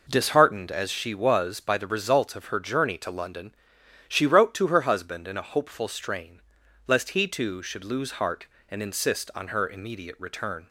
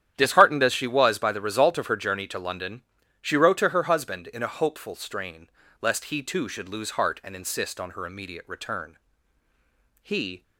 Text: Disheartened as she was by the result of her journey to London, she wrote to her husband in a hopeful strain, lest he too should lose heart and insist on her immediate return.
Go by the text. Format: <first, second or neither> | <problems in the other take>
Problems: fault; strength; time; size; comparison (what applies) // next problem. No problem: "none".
first | starts louder than the rest; strong; until 1.1 s; 10 dB // goes on to say "He"; slight; from 10.0 s on; 0.40 s long